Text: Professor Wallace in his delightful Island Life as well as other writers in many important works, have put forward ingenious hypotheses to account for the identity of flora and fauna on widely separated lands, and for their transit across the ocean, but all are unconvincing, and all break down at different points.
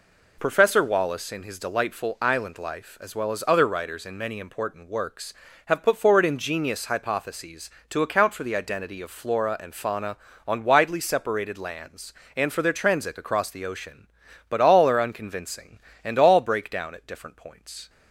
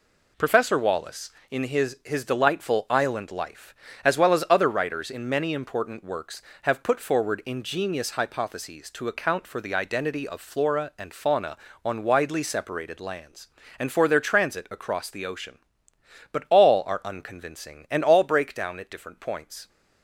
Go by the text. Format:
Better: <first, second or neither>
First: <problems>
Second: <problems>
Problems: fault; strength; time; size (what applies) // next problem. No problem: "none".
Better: first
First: none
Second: says "his" twice; at 2.0 s